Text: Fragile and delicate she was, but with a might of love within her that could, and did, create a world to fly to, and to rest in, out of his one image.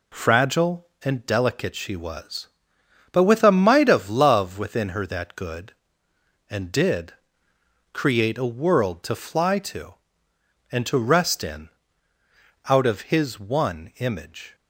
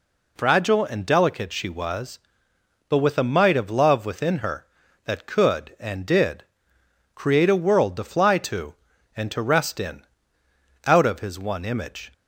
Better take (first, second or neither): second